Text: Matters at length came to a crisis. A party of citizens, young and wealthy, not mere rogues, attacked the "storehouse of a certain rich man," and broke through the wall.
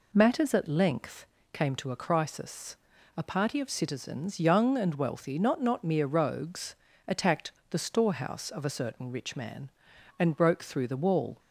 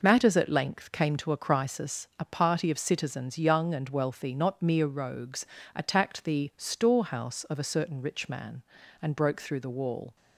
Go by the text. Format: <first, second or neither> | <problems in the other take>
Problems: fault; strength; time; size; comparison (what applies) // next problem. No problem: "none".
second | pauses between "length" and "came"; slight; at 1.2 s; 0.28 s long // says "not" twice; at 5.6 s // pauses between "attacked" and "the"; slight; at 7.5 s; 0.20 s long